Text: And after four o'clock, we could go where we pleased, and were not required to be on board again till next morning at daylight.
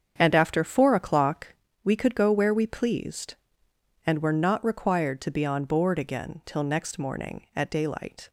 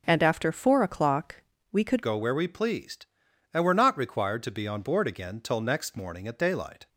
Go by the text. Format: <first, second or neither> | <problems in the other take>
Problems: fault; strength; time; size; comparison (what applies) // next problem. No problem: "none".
first | starts louder than the rest; until 1.0 s; 7 dB; strong in the first // changes voice at "go"; from 2.0 s on; 4.8 s long